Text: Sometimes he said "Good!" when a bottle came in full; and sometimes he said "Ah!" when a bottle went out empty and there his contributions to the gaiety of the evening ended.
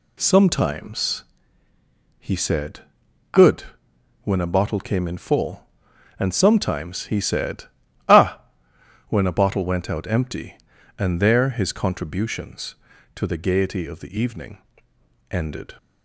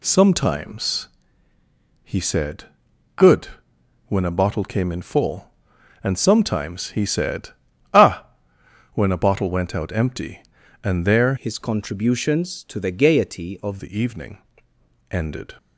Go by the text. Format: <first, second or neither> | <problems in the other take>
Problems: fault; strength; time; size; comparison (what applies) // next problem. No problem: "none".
first | pauses between "Sometimes" and "he"; noticeable; at 1.0 s; 0.96 s long; noticeable in the first // pauses between "said" and "Good"; noticeable; at 2.6 s; 0.50 s long; noticeable in the first // pauses between "said" and "Ah"; at 7.5 s; 0.44 s long; also in the first // changes voice from "his" to "of"; from 11.3 to 13.7 s; 2.4 s long // pauses between "evening" and "ended"; noticeable; at 14.3 s; 0.72 s long; noticeable in the first